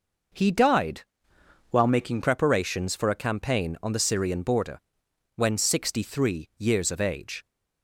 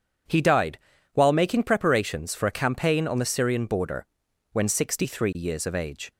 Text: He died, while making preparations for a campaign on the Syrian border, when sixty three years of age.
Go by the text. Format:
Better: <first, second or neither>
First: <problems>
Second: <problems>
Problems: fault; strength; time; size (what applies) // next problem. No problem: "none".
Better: second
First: changes voice from "while" to "making"; from 1.7 to 2.2 s; 0.5 s long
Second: none